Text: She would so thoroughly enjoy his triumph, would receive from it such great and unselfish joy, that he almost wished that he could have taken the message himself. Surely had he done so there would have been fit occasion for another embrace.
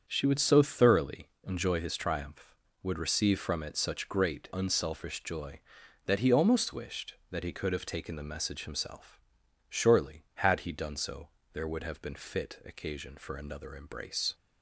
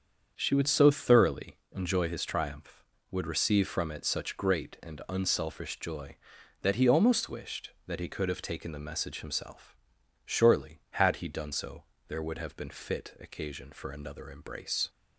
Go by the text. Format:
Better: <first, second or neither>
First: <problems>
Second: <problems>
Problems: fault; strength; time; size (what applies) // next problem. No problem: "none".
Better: second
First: starts louder than the rest; strong; until 1.0 s; 7.5 dB // pauses between "thoroughly" and "enjoy"; slight; at 1.2 s; 0.16 s long // skips "and"; at 4.5 s // pauses between "so" and "there"; slight; at 11.2 s; 0.24 s long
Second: starts louder than the rest; strong; until 1.3 s; 7.5 dB // pauses between "thoroughly" and "enjoy"; slight; at 1.5 s; 0.16 s long // pauses between "so" and "there"; slight; at 11.8 s; 0.24 s long